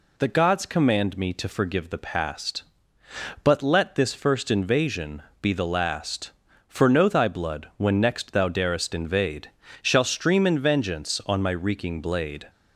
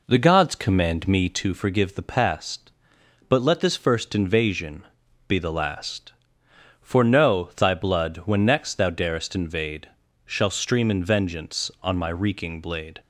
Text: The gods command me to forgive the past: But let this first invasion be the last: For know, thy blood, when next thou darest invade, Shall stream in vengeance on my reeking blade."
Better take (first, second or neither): first